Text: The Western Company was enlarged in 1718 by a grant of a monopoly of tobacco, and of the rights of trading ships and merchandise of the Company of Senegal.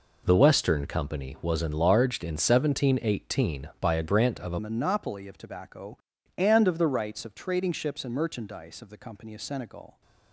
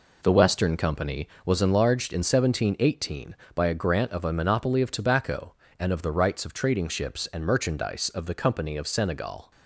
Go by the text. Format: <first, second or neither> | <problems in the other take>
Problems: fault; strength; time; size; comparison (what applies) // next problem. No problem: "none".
second | changes voice at "monopoly"; from 4.5 s on; 5.5 s long